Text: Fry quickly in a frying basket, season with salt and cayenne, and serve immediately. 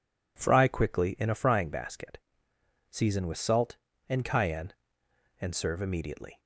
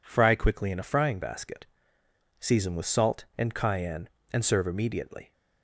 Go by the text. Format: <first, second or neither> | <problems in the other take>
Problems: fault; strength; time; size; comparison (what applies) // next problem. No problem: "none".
neither | none